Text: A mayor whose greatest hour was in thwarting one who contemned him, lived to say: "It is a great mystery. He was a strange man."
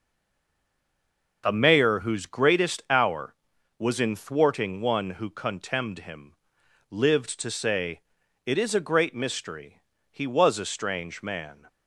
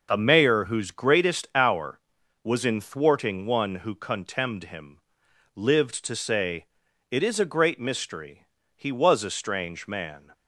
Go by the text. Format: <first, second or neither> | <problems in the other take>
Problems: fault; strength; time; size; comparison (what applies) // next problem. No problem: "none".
second | stays silent before the first word; noticeable; until 1.4 s; 1.4 s long // starts louder than the rest; noticeable; until 2.4 s; 6 dB; noticeable in the second